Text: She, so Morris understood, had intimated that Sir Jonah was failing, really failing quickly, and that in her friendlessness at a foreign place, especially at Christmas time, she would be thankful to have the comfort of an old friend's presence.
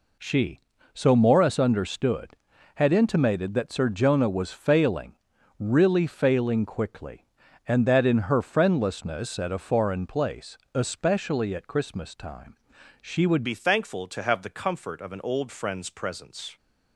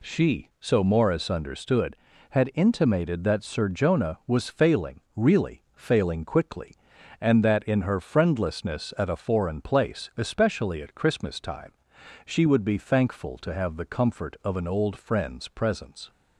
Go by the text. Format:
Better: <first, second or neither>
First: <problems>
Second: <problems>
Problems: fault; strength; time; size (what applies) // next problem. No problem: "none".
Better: second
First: changes voice at "be"; from 13.4 s on; 3.1 s long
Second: none